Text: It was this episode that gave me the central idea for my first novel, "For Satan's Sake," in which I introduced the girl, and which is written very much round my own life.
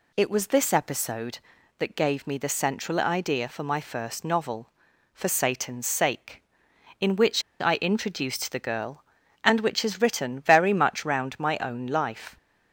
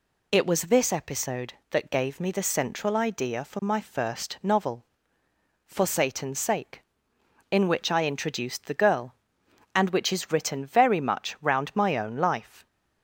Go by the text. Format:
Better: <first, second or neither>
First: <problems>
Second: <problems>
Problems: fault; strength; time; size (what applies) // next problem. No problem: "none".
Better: second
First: pauses between "which" and "I"; slight; at 7.4 s; 0.18 s long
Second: none